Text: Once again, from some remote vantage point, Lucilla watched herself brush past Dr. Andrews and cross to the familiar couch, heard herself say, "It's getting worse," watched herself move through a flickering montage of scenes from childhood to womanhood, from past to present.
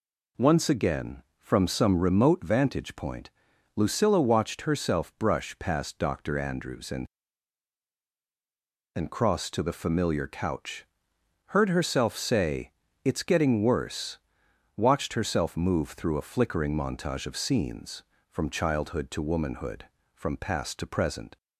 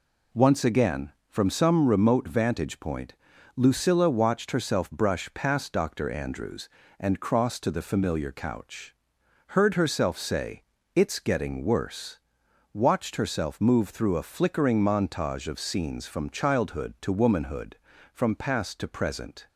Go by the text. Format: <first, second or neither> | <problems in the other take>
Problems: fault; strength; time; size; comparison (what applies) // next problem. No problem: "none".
second | says "and" twice; at 8.9 s